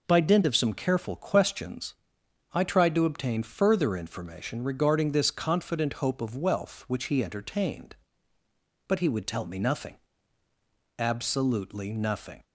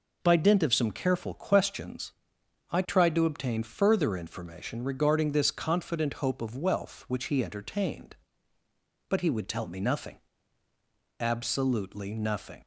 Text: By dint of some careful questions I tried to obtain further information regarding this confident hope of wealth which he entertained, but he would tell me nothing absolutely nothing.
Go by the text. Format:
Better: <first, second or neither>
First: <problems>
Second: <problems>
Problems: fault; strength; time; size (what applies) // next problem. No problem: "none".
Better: neither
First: pauses between "questions" and "I"; noticeable; at 1.9 s; 0.60 s long // pauses between "nothing" and "absolutely"; at 9.9 s; 1.0 s long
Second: pauses between "questions" and "I"; noticeable; at 2.1 s; 0.60 s long // pauses between "nothing" and "absolutely"; at 10.1 s; 1.0 s long